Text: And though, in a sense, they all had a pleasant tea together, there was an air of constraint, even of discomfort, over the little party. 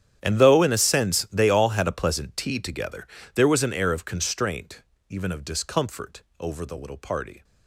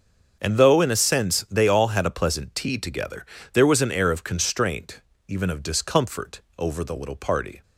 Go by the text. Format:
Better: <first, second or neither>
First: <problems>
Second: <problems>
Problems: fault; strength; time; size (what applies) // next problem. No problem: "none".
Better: second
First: gets quieter; strong; throughout; 19.5 dB // starts louder than the rest; strong; until 1.2 s; 10 dB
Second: starts louder than the rest; until 1.4 s; 6.5 dB